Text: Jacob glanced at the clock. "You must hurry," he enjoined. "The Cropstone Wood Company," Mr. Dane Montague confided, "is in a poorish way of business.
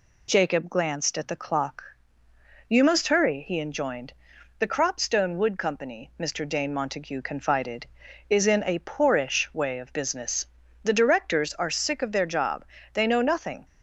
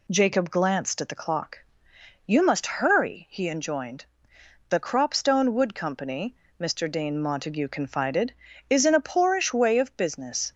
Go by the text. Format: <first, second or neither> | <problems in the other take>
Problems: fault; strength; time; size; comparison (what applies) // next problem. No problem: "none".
second | goes on to say "The directors are sick of their job They know nothing"; strong; from 10.8 s on; 2.8 s long